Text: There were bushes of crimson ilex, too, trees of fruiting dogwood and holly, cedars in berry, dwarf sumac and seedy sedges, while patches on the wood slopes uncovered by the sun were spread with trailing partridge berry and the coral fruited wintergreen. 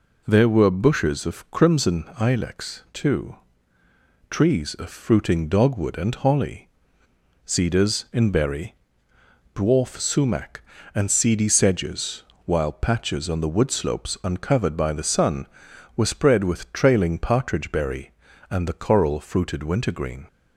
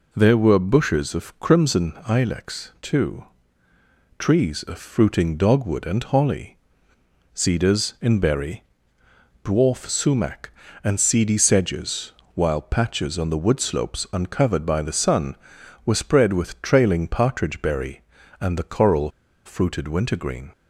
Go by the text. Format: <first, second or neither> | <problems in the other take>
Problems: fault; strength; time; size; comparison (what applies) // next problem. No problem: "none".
first | pauses between "coral" and "fruited"; at 19.0 s; 0.36 s long